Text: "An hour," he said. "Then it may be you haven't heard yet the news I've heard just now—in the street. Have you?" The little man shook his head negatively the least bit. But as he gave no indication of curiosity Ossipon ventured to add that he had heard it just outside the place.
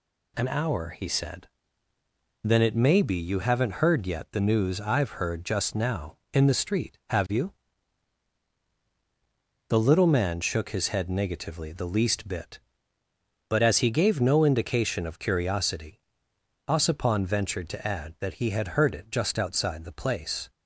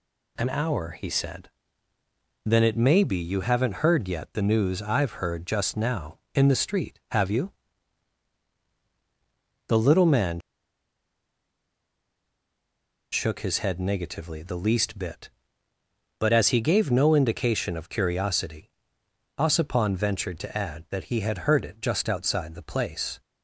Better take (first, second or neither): first